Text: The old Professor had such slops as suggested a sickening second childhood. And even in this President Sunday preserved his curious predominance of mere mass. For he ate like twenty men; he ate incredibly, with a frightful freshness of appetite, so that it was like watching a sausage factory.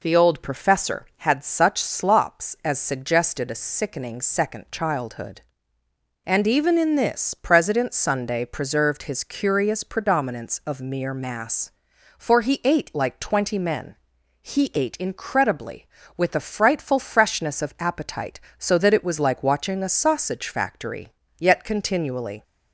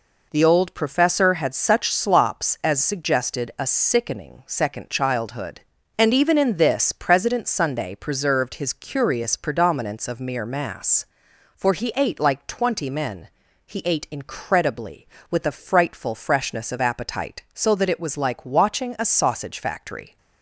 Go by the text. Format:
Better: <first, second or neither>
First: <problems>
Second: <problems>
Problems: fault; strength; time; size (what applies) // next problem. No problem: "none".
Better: second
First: goes on to say "Yet continually"; noticeable; from 21.3 s on; 1.0 s long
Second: none